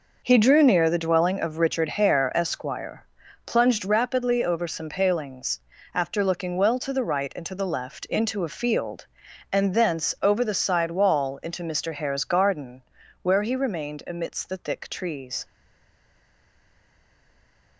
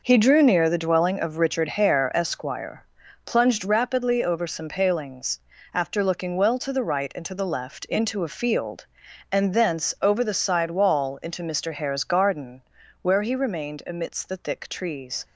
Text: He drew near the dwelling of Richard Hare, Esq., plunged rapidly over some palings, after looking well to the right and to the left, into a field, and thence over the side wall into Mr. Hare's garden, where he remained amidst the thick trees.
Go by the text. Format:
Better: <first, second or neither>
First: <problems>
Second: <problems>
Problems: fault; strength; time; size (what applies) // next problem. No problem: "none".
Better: second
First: stays silent after the last word; from 15.4 s on; 2.3 s long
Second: none